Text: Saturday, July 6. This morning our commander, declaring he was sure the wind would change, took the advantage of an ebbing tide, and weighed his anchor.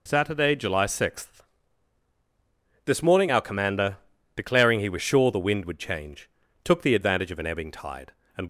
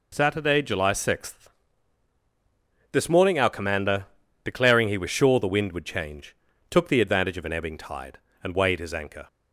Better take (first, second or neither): second